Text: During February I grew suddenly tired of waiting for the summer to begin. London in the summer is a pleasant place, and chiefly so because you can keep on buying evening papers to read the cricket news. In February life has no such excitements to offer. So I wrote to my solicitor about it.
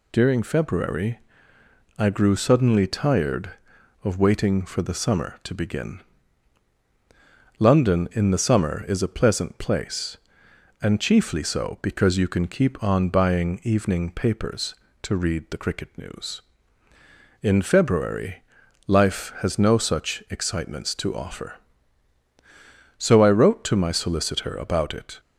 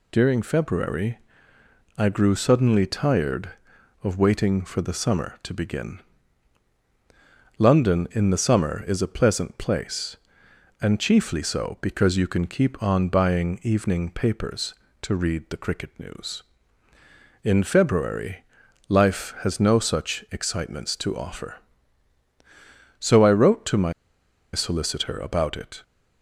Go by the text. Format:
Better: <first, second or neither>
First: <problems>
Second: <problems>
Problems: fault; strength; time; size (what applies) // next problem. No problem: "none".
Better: first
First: pauses between "February" and "I"; noticeable; at 1.1 s; 0.80 s long // pauses between "February" and "life"; noticeable; at 18.4 s; 0.46 s long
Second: pauses between "February" and "I"; noticeable; at 1.1 s; 0.80 s long // pauses between "February" and "life"; noticeable; at 18.4 s; 0.46 s long // pauses between "my" and "solicitor"; noticeable; at 23.9 s; 0.61 s long